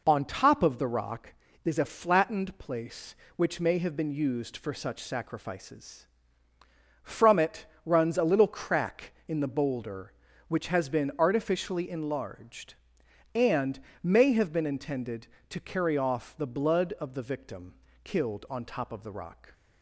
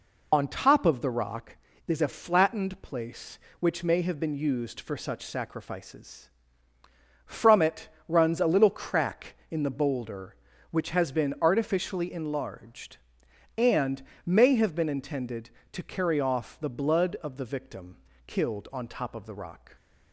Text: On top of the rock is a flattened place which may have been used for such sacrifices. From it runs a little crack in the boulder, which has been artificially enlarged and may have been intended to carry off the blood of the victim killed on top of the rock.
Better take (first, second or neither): first